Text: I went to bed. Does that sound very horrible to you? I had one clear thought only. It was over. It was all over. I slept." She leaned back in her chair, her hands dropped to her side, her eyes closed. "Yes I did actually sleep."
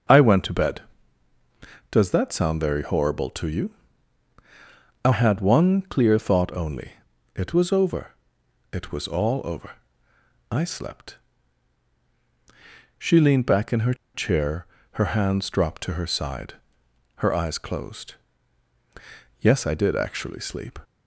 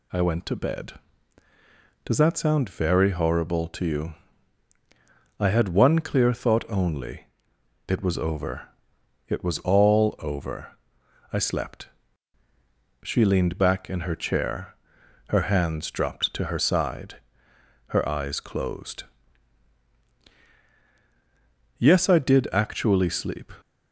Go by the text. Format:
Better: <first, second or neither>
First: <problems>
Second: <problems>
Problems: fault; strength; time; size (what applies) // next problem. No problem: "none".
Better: second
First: starts louder than the rest; until 2.2 s; 6.5 dB // pauses between "her" and "chair"; slight; at 13.9 s; 0.20 s long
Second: none